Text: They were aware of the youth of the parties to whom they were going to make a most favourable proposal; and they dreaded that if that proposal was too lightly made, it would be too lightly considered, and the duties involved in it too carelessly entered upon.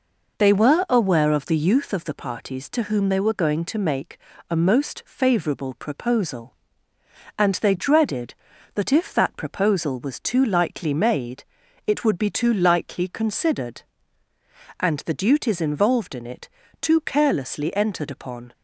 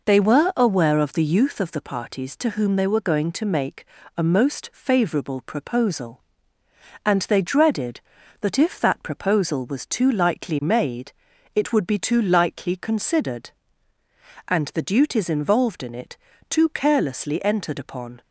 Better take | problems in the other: neither | pauses between "make" and "a"; slight; the same in both // pauses between "it" and "too"; slight; the same in both

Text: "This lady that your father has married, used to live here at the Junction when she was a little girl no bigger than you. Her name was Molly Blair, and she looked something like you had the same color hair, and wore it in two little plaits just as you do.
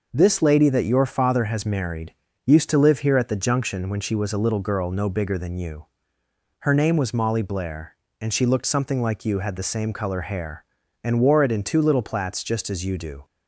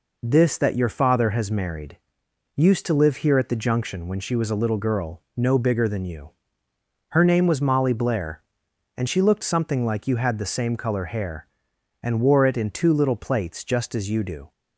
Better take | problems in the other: first | skips "lady"; at 0.5 s // pauses between "girl" and "no"; slight; at 5.2 s; 0.16 s long

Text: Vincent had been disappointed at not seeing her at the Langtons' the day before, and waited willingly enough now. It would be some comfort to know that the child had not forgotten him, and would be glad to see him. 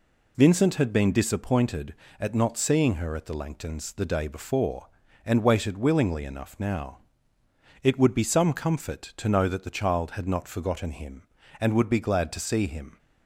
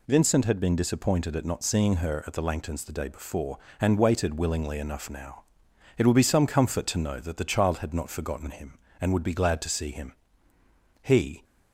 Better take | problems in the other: first | goes on to say "He"; slight; from 11.0 s on; 0.42 s long

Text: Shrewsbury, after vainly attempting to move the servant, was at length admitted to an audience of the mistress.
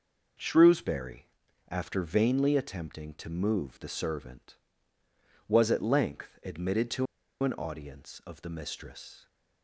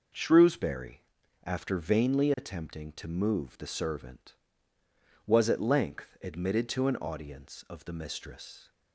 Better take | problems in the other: second | pauses between "to" and "an"; at 7.0 s; 0.37 s long

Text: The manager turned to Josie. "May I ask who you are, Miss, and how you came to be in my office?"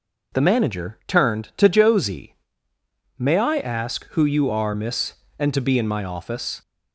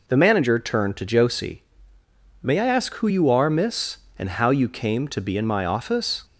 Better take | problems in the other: second | skips "how you came"; at 5.5 s

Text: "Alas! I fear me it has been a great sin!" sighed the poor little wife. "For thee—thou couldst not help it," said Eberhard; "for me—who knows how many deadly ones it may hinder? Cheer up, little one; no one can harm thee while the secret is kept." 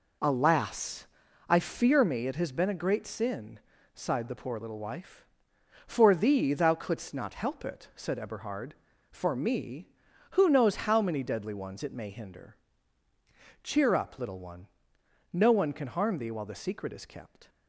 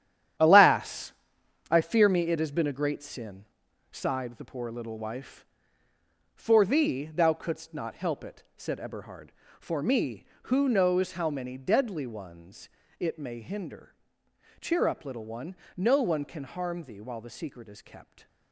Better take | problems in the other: first | gets quieter; strong; throughout; 9 dB // pauses between "ones" and "it"; slight; at 12.6 s; 0.30 s long

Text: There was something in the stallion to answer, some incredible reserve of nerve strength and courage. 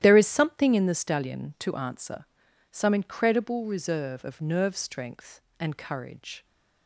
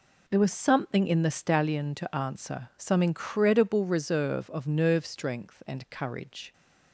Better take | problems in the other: second | starts louder than the rest; strong; until 1.0 s; 12 dB // says "is" for "was"; at 0.1 s

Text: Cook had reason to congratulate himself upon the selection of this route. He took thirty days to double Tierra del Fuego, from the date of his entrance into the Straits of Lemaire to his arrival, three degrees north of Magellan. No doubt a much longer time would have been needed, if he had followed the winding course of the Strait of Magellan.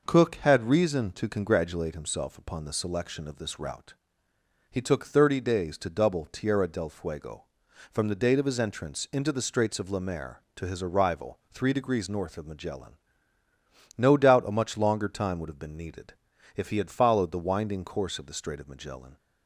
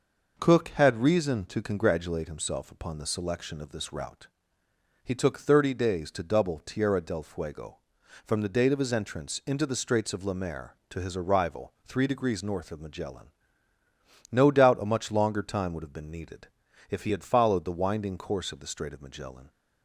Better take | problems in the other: neither | none

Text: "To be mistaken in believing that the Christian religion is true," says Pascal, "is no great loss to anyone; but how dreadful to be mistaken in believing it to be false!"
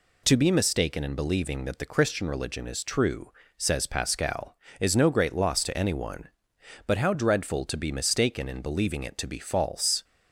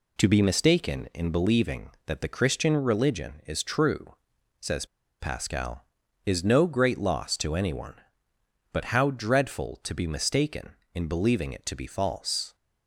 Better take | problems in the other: first | pauses between "says" and "Pascal"; slight; at 4.8 s; 0.35 s long

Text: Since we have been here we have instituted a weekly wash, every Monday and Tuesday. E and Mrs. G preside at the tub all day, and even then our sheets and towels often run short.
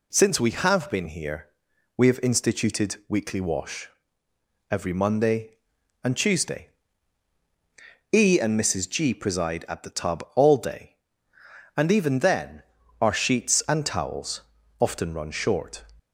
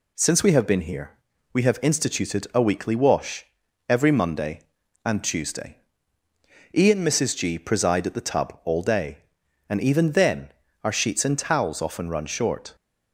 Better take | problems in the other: second | pauses between "here" and "we"; noticeable; at 1.4 s; 0.50 s long; also in the second // skips "a"; at 3.0 s // pauses between "then" and "our"; at 12.6 s; 0.38 s long; slight in the second // pauses between "towels" and "often"; at 14.4 s; 0.40 s long

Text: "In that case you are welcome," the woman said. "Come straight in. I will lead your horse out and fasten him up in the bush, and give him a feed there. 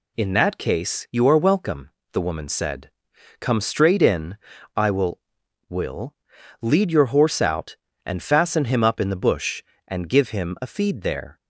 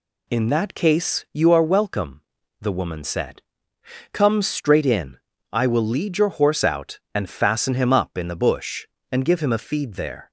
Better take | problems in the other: second | says "will" twice; at 5.6 s

